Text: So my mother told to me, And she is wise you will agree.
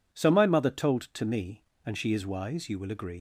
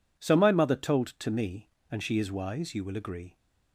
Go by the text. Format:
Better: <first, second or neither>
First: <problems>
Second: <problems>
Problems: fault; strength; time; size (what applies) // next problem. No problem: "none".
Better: second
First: leaves "agree" unfinished; at 3.1 s; 115 ms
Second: none